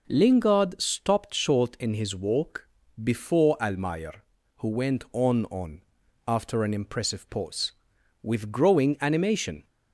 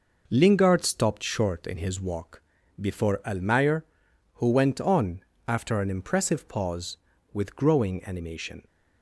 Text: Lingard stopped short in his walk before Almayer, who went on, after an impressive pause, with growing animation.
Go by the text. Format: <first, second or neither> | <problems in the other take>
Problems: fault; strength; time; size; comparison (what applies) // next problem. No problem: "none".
second | pauses between "walk" and "before"; slight; at 2.6 s; 0.34 s long; also in the second // says "on" twice; at 5.4 s